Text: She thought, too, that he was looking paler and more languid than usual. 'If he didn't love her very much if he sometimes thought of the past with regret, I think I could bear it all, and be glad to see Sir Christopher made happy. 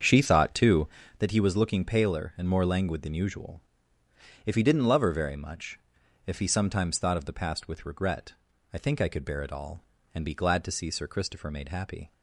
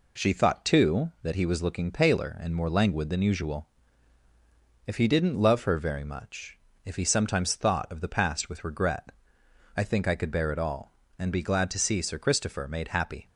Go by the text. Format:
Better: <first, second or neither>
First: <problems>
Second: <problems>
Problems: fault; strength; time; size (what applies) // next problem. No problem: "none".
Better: second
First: starts louder than the rest; strong; until 1.2 s; 7 dB // pauses between "much" and "if"; noticeable; at 5.7 s; 0.48 s long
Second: pauses between "much" and "if"; slight; at 6.5 s; 0.28 s long